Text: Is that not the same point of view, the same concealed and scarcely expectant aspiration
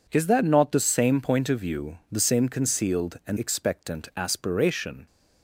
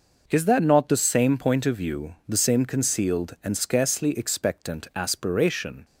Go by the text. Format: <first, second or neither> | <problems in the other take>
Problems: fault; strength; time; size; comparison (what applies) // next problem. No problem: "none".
second | skips "scarcely"; at 3.3 s